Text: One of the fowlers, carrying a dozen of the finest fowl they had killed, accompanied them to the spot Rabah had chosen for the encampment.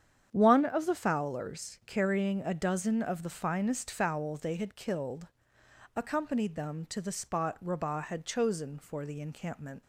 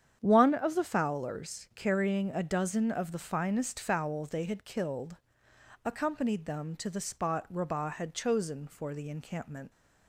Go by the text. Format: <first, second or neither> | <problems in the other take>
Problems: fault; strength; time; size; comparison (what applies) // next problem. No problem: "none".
neither | starts louder than the rest; strong; the same in both